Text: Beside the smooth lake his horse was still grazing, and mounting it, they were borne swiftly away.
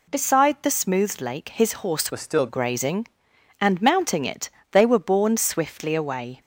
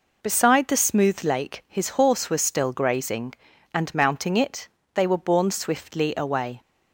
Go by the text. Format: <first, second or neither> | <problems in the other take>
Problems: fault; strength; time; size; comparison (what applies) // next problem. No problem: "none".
second | changes voice from "was" to "still"; from 2.1 to 2.4 s; 0.3 s long